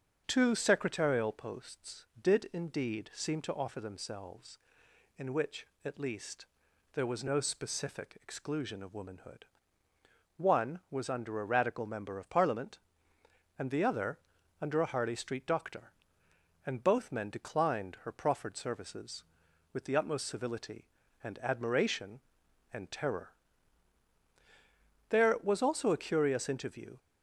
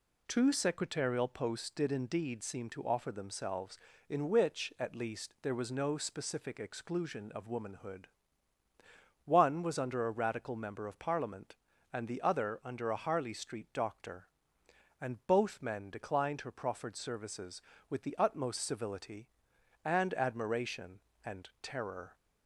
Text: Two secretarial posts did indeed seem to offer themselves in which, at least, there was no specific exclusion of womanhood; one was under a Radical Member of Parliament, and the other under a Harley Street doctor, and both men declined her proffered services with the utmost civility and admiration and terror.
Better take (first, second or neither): second